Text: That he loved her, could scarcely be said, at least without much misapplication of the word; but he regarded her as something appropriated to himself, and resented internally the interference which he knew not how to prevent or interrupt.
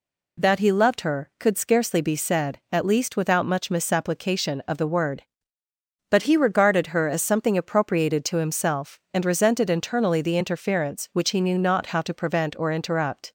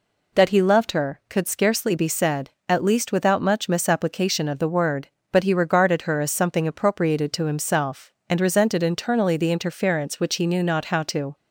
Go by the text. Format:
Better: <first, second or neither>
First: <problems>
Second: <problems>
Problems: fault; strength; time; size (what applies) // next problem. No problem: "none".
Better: first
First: none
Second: stops before "prevent or interrupt"; at 11.3 s